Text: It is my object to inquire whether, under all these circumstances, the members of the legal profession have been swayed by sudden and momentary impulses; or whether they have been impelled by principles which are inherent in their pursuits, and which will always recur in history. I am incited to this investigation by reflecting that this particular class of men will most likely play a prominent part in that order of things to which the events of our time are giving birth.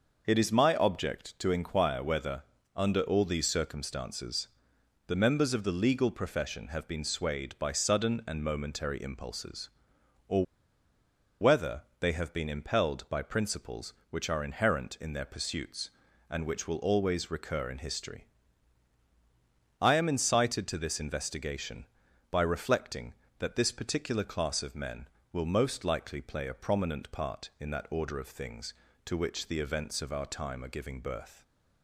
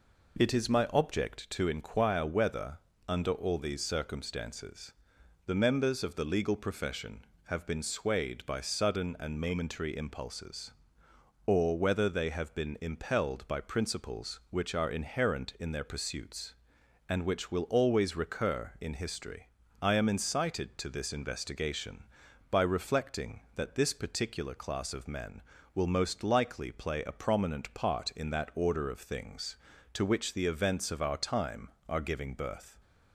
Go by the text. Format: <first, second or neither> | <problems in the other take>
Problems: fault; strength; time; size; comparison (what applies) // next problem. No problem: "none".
second | starts louder than the rest; noticeable; until 1.2 s; 6 dB // pauses between "or" and "whether"; noticeable; at 10.4 s; 0.98 s long // pauses between "whether" and "they"; slight; at 11.8 s; 0.16 s long